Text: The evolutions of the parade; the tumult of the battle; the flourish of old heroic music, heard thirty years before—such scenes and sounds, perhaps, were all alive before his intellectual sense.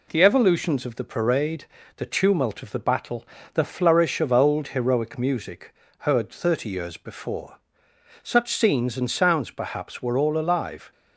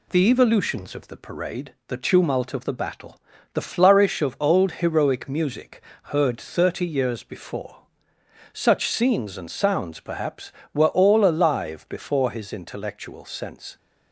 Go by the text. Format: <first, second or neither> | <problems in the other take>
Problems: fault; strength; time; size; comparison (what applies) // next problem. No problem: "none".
second | stops before "before his intellectual sense"; at 10.9 s